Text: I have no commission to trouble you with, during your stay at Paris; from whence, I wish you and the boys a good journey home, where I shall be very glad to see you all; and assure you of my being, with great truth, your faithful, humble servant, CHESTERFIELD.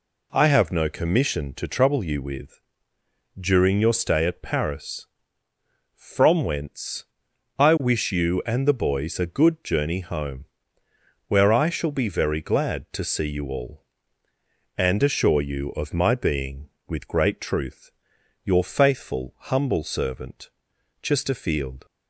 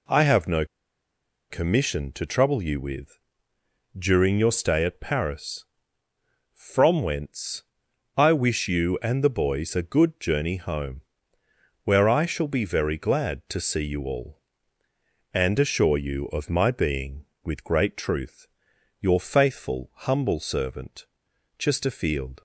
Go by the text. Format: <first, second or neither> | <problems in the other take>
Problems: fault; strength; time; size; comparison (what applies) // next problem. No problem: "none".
first | pauses between "no" and "commission"; noticeable; at 0.6 s; 0.85 s long